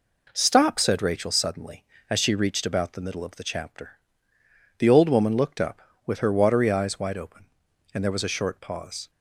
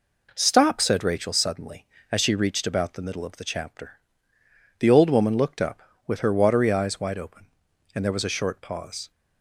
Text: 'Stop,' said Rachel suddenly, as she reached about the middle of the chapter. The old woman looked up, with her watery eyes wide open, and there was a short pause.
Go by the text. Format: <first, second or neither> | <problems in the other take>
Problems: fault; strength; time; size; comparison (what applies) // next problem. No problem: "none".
neither | none